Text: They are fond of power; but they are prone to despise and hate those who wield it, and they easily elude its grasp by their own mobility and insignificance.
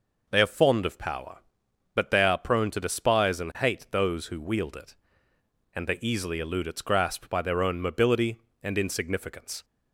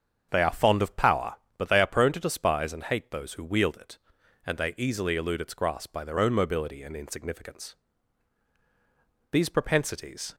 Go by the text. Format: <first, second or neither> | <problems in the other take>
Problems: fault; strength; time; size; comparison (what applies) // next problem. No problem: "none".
first | starts louder than the rest; strong; until 1.3 s; 7 dB // goes on to say "These propensities"; noticeable; from 9.3 s on; 1.0 s long